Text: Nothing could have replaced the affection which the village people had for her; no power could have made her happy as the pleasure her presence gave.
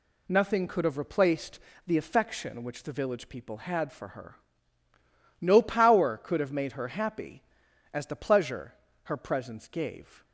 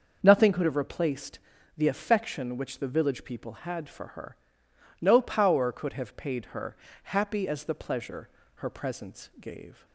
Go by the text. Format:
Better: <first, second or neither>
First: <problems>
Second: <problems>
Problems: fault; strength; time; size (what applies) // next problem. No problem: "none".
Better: first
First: pauses between "replaced" and "the"; slight; at 1.6 s; 0.26 s long // pauses between "pleasure" and "her"; slight; at 8.7 s; 0.30 s long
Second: starts louder than the rest; until 1.2 s; 6.5 dB // pauses between "replaced" and "the"; at 1.3 s; 0.38 s long // says "paid" for "made"; at 6.1 s // pauses between "her" and "happy"; slight; at 6.7 s; 0.28 s long // pauses between "pleasure" and "her"; slight; at 8.2 s; 0.26 s long